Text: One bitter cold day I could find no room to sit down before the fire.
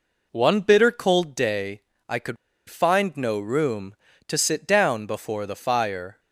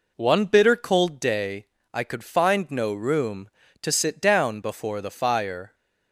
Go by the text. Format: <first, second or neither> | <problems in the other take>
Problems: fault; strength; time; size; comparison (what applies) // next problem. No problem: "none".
second | pauses between "day" and "I"; slight; at 1.8 s; 0.26 s long; slight in the second // pauses between "could" and "find"; slight; at 2.3 s; 0.33 s long